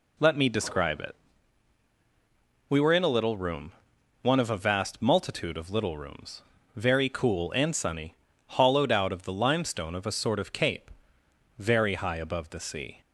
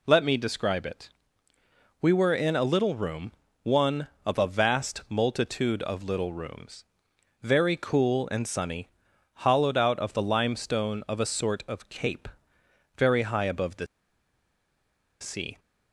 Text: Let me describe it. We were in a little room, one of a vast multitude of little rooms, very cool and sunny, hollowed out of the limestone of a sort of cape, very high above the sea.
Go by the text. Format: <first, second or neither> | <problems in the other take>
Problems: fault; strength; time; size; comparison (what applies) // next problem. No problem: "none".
first | pauses between "the" and "sea"; strong; at 13.8 s; 1.3 s long